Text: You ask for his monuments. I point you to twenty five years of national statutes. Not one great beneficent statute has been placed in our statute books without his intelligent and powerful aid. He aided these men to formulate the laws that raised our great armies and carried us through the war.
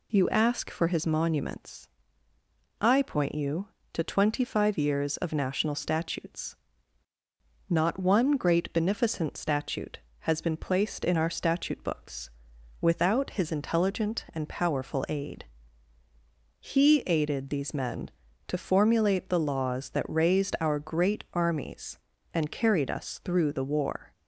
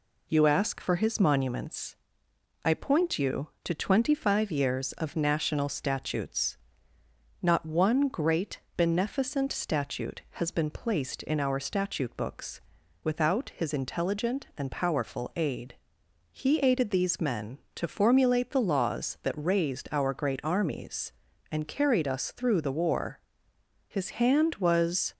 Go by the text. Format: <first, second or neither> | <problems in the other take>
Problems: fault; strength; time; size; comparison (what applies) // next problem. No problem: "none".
first | pauses between "great" and "beneficent"; slight; at 8.5 s; 0.16 s long // pauses between "books" and "without"; at 12.6 s; 0.44 s long; noticeable in the first // goes on to say "His hand was"; noticeable; from 23.8 s on; 1.2 s long